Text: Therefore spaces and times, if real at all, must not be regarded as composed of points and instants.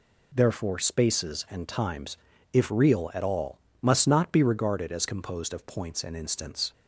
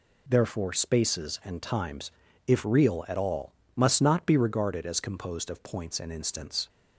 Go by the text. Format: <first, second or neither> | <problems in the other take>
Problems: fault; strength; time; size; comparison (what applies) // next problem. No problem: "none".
neither | none